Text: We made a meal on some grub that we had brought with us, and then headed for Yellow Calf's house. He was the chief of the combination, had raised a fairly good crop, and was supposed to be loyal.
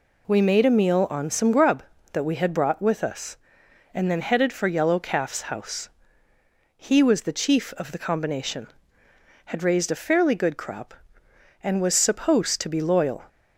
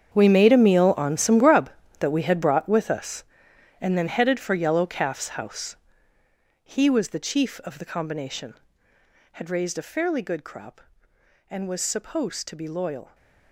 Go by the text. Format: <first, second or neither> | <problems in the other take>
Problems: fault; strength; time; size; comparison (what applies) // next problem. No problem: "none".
first | gets quieter; strong; throughout; 15.5 dB